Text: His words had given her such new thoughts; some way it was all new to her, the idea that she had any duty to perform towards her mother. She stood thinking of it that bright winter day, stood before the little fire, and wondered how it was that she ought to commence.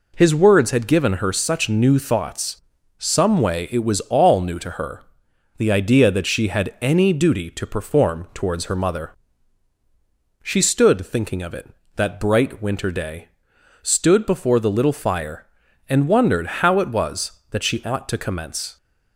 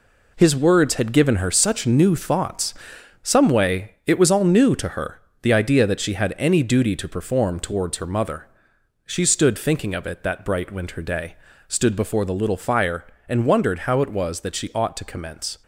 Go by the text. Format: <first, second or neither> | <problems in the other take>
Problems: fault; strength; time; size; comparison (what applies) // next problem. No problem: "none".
first | gets quieter; strong; throughout; 7.5 dB